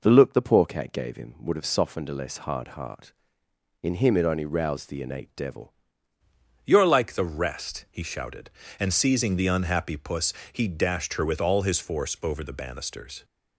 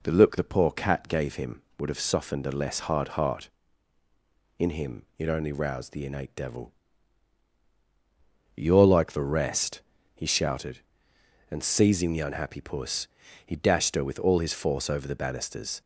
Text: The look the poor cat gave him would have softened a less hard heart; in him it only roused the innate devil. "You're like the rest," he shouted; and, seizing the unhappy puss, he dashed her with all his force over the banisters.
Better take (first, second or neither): second